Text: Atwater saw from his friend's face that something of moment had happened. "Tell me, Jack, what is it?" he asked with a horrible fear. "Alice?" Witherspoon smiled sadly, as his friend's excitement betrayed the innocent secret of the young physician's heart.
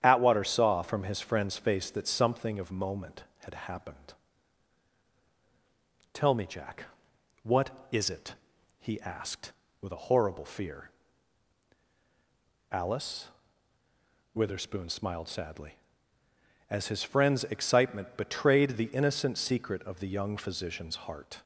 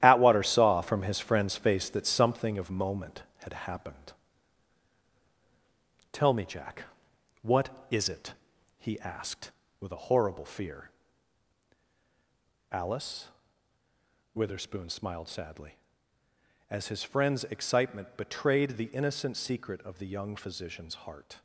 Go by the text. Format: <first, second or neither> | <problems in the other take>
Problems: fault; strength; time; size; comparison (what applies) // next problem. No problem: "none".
first | gets quieter; strong; throughout; 8 dB // starts louder than the rest; strong; until 1.0 s; 12 dB; strong in the first